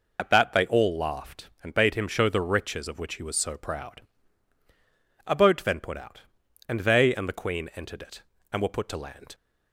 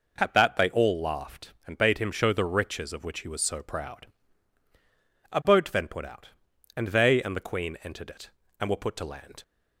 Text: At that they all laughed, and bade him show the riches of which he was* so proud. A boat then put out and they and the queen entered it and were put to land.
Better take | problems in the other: second | loses the start of "At"; at 0.1 s; 55 ms

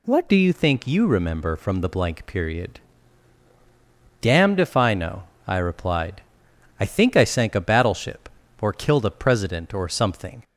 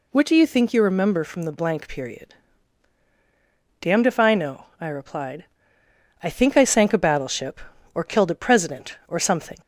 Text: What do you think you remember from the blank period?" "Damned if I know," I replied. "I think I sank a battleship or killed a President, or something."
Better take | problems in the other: second | changes voice at "do"; from 0.2 s on; 10.2 s long

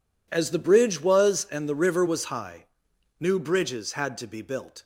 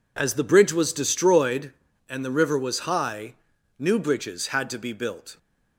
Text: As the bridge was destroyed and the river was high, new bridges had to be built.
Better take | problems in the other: second | skips "destroyed"; at 1.4 s

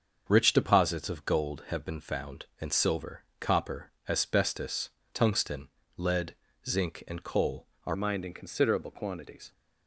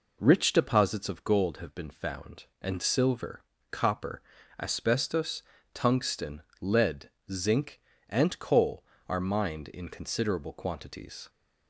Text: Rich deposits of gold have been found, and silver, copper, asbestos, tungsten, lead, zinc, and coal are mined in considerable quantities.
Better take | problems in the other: second | starts louder than the rest; until 1.2 s; 7 dB // changes voice at "mined"; from 7.9 s on; 1.6 s long

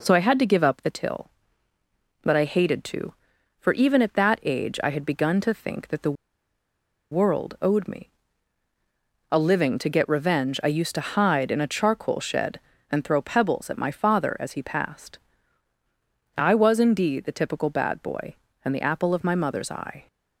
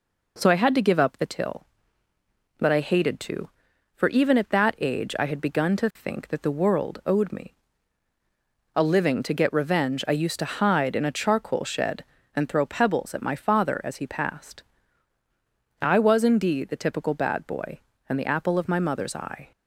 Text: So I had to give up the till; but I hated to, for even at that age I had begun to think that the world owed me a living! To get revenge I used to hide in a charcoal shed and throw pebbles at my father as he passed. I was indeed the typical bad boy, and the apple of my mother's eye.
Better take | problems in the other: second | pauses between "the" and "world"; noticeable; at 6.1 s; 0.97 s long // pauses between "me" and "a"; at 8.0 s; 1.2 s long; also in the second

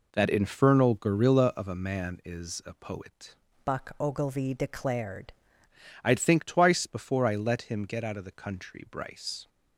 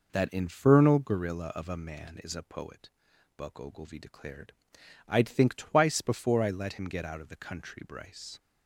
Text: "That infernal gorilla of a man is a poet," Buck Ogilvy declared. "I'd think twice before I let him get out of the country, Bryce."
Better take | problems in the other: second | changes voice from "Buck" to "declared"; from 3.6 to 5.3 s; 1.7 s long

